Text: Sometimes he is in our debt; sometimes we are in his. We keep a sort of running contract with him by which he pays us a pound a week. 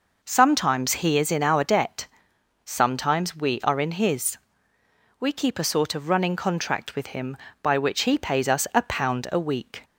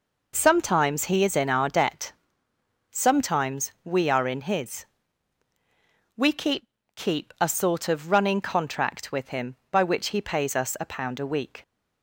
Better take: first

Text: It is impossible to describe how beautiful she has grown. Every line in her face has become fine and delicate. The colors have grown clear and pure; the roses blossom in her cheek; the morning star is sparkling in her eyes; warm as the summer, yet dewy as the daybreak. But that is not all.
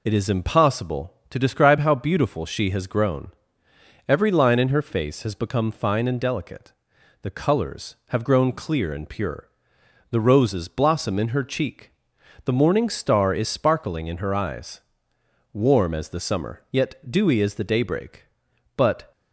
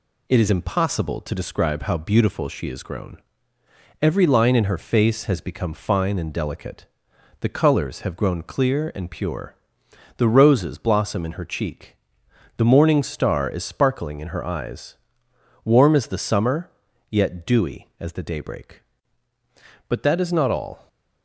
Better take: second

